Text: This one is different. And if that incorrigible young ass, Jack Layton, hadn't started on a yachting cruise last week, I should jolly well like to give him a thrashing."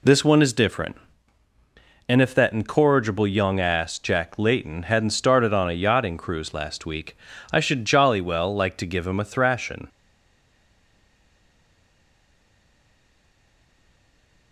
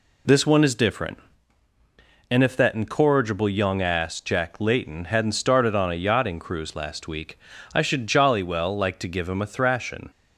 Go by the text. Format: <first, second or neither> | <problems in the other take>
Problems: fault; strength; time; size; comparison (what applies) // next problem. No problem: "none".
second | stays silent after the last word; strong; from 9.8 s on; 4.7 s long